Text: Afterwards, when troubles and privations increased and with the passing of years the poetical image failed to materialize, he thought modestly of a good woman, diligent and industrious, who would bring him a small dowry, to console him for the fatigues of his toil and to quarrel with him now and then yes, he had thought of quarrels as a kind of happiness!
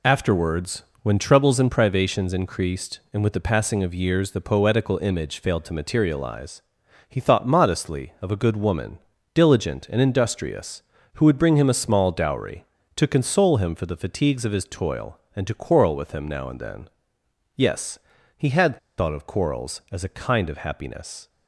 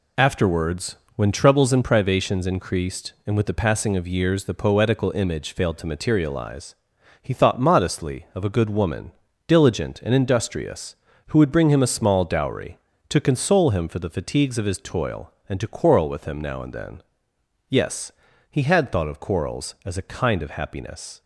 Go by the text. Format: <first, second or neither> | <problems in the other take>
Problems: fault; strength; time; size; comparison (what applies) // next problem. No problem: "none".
second | pauses between "then" and "yes"; noticeable; at 16.8 s; 0.68 s long; noticeable in the second // pauses between "had" and "thought"; slight; at 18.7 s; 0.19 s long